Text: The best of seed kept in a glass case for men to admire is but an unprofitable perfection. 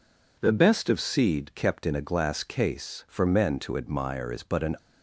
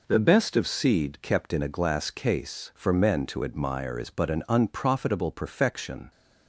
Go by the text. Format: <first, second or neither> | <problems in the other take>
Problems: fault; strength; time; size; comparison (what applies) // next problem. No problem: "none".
second | stops before "unprofitable perfection"; at 4.7 s